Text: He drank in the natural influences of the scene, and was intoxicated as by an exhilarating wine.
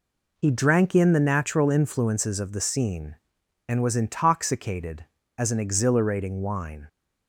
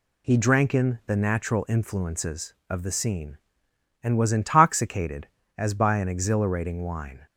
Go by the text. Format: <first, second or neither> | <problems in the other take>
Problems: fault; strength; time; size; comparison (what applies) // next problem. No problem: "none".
second | skips "by"; at 5.4 s